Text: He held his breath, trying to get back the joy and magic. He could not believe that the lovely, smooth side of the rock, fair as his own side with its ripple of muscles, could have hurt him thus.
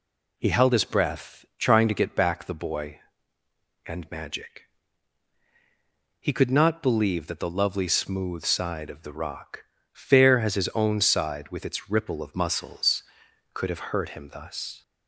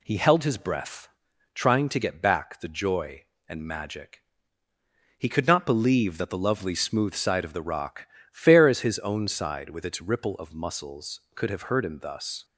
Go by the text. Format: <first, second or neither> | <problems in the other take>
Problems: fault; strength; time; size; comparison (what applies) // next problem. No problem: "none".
second | says "boy" for "joy"; at 2.5 s